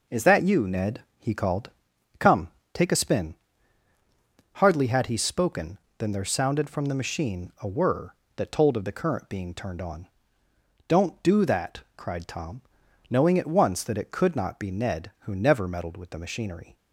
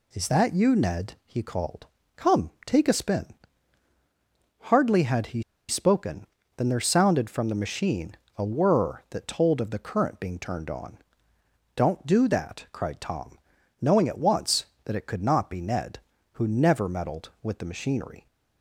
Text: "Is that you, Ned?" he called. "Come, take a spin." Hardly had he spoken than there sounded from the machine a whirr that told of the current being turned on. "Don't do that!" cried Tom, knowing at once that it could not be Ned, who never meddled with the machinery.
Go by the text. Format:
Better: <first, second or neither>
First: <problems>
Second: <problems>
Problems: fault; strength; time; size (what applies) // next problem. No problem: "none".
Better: first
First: none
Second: pauses between "he" and "spoken"; slight; at 5.4 s; 0.28 s long // pauses between "machine" and "a"; slight; at 8.1 s; 0.20 s long